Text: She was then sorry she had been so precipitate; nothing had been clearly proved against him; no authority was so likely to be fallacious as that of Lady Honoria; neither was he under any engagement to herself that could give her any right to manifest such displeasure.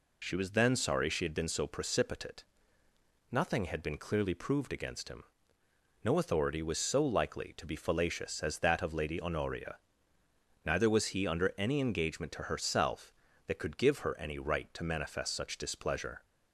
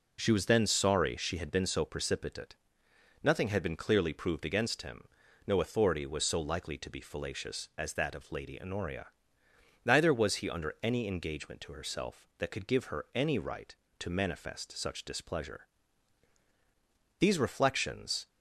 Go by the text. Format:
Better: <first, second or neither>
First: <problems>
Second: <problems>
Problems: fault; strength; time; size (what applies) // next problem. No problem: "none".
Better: first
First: none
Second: goes on to say "These reflections"; noticeable; from 17.1 s on; 1.0 s long